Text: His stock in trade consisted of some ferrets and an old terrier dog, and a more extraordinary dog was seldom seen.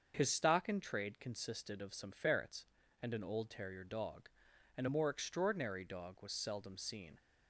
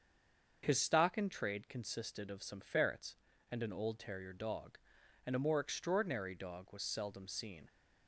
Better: first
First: starts louder than the rest; until 1.1 s; 6.5 dB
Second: stays silent before the first word; slight; until 0.6 s; 0.6 s long // starts louder than the rest; until 1.6 s; 6.5 dB

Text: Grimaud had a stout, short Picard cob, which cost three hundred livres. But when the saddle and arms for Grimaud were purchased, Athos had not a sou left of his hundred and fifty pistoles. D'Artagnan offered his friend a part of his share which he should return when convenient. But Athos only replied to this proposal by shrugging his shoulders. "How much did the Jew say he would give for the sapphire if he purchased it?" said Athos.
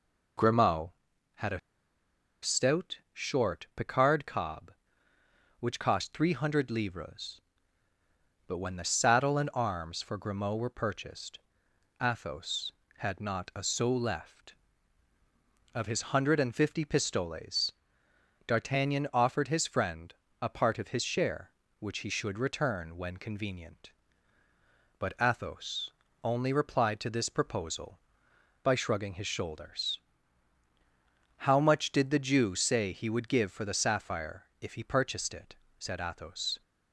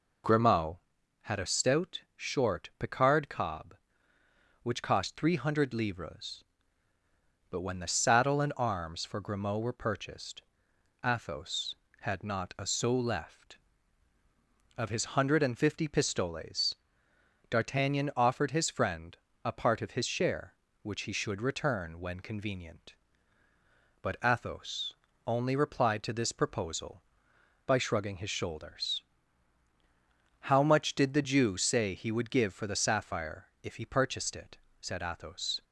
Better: second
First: pauses between "a" and "stout"; noticeable; at 1.5 s; 0.83 s long // pauses between "friend" and "a"; slight; at 20.1 s; 0.26 s long // pauses between "Athos" and "only"; slight; at 25.9 s; 0.32 s long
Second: pauses between "friend" and "a"; slight; at 19.1 s; 0.26 s long // pauses between "Athos" and "only"; slight; at 24.9 s; 0.32 s long

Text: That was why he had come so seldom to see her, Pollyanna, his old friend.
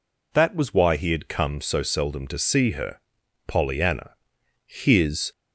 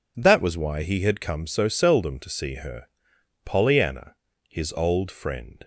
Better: second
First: stops before "old friend"; at 5.3 s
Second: none

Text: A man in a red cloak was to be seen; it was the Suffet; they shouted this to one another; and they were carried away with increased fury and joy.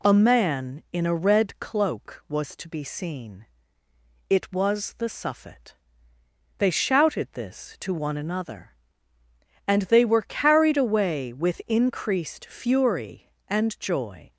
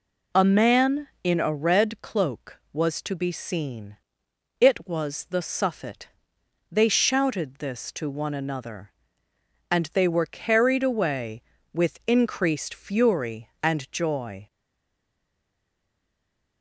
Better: first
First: none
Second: stays silent after the last word; from 14.4 s on; 2.2 s long

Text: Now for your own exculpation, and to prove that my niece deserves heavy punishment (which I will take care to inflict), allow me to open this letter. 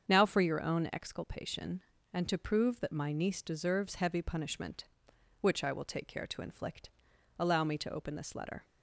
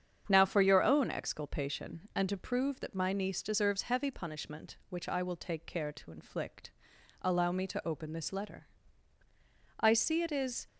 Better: first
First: starts louder than the rest; strong; until 1.1 s; 7 dB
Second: starts louder than the rest; strong; until 1.2 s; 8 dB // goes on to say "I see it is"; noticeable; from 9.8 s on; 0.86 s long

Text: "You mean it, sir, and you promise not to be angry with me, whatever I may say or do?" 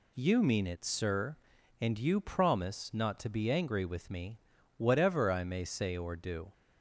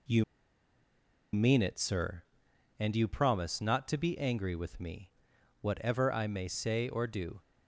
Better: first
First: none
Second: pauses between "You" and "mean"; at 0.2 s; 1.1 s long

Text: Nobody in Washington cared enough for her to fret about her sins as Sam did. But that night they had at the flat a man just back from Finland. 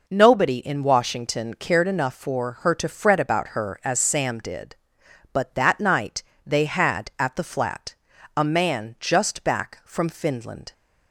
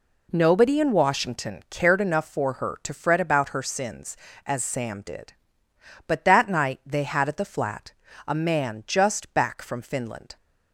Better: second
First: skips "sins"; at 3.8 s // pauses between "night" and "they"; slight; at 6.2 s; 0.22 s long // pauses between "flat" and "a"; at 7.9 s; 0.42 s long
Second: pauses between "flat" and "a"; slight; at 7.9 s; 0.36 s long

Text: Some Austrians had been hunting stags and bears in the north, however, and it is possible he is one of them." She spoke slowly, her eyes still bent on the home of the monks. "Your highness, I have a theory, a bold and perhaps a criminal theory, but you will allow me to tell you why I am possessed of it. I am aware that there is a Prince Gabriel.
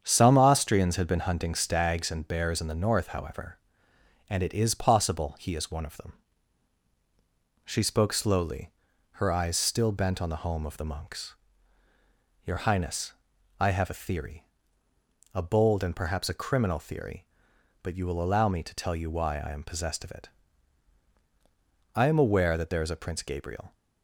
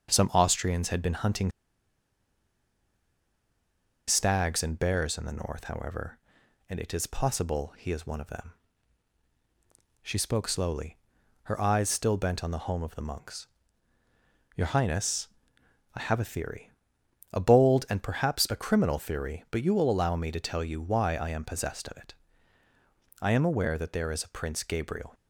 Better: first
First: starts louder than the rest; strong; until 1.0 s; 8 dB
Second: starts louder than the rest; until 1.1 s; 7 dB // pauses between "hunting" and "stags"; strong; at 1.5 s; 2.5 s long

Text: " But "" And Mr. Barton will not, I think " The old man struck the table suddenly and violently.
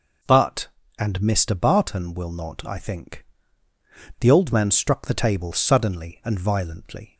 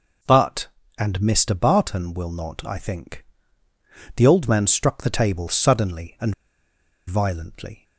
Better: first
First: none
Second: pauses between "and" and "violently"; noticeable; at 6.3 s; 0.75 s long

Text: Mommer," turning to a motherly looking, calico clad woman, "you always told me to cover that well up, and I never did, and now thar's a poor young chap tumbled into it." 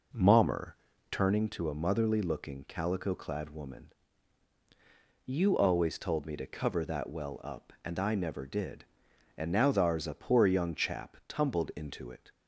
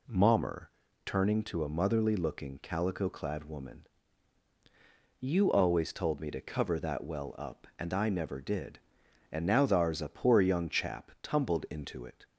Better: second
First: starts louder than the rest; noticeable; until 1.4 s; 4.5 dB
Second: none

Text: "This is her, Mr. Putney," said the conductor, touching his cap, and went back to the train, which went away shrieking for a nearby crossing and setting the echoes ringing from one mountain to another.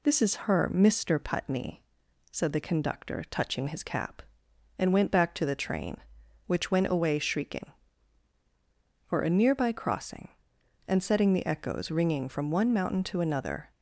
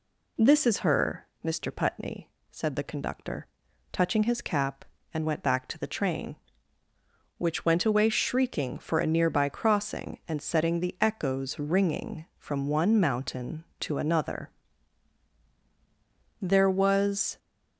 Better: first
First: none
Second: goes on to say "There was"; noticeable; from 16.4 s on; 0.96 s long

